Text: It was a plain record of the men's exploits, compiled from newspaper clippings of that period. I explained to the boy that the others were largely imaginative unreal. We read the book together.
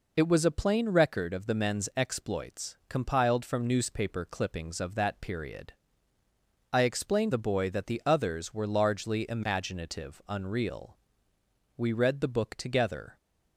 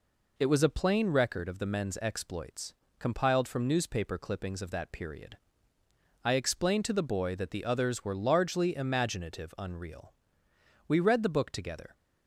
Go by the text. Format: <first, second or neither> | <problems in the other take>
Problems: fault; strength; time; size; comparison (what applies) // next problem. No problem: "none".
second | skips "to"; at 7.3 s